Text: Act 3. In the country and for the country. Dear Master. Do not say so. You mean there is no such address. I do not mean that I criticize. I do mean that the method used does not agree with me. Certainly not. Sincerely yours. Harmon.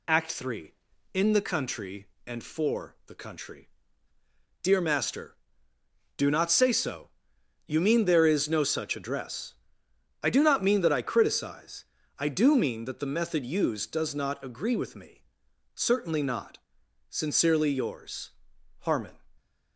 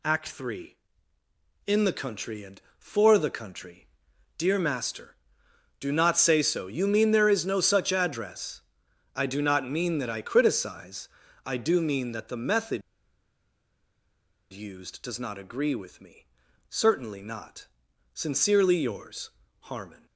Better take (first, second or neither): first